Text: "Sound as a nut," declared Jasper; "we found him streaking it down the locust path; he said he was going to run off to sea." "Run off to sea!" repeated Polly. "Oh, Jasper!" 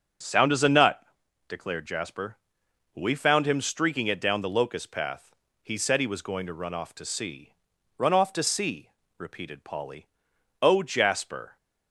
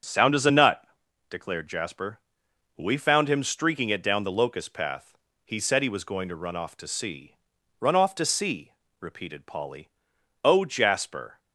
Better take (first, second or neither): neither